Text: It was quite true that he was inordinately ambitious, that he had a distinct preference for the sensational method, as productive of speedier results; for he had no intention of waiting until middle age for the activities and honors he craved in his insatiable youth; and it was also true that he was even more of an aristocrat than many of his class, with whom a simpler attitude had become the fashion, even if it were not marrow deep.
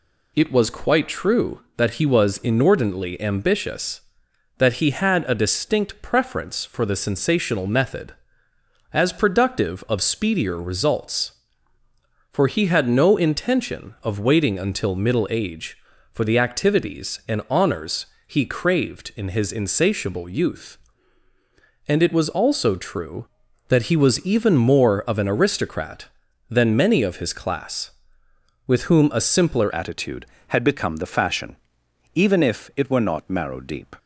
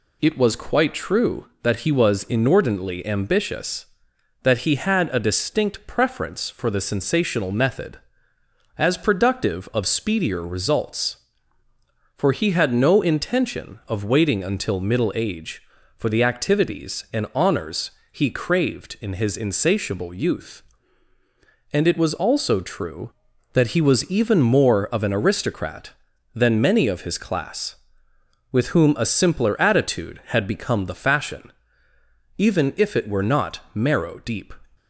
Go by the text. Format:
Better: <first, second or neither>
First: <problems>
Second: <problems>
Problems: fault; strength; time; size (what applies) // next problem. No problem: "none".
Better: second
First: pauses between "honors" and "he"; slight; at 18.0 s; 0.20 s long // changes voice at "attitude"; from 29.7 s on; 4.2 s long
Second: pauses between "honors" and "he"; slight; at 17.9 s; 0.20 s long